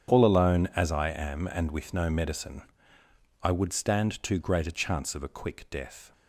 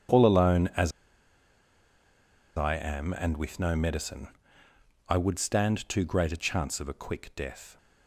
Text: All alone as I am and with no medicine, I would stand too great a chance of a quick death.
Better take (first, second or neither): first